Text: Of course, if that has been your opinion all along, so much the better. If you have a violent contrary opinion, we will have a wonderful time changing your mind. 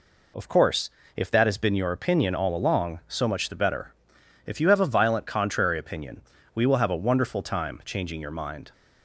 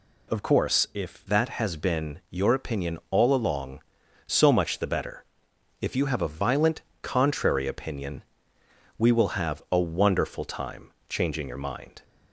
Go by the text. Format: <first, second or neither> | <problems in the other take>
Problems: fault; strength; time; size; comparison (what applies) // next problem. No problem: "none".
first | changes voice at "that"; from 1.2 s on; 10.8 s long // pauses between "violent" and "contrary"; slight; at 6.8 s; 0.18 s long // pauses between "time" and "changing"; slight; at 10.8 s; 0.20 s long